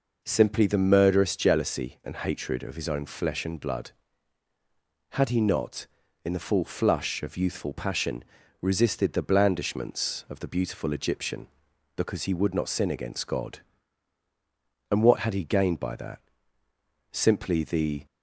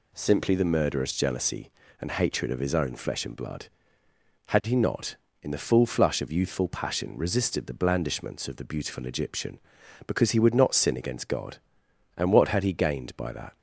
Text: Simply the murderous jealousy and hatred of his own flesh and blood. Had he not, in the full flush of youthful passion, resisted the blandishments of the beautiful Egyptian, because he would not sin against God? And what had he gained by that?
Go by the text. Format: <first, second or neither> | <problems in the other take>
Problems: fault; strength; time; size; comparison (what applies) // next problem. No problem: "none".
second | goes on to say "Simply the"; noticeable; from 17.1 s on; 0.94 s long